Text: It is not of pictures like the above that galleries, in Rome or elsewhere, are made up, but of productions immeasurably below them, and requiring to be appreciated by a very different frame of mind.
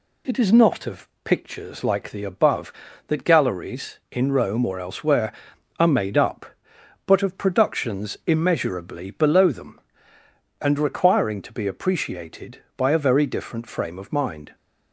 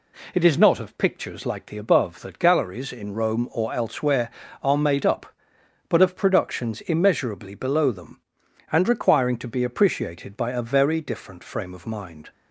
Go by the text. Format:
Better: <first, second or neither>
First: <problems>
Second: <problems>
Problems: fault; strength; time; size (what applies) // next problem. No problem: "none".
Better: neither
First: none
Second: none